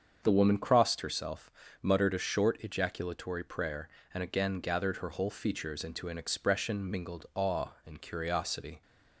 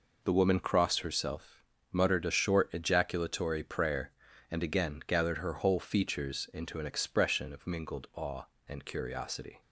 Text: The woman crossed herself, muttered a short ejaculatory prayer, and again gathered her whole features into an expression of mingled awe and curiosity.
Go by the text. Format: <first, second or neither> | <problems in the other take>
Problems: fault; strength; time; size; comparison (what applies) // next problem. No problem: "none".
second | starts louder than the rest; until 1.2 s; 7 dB // skips "of"; at 6.8 s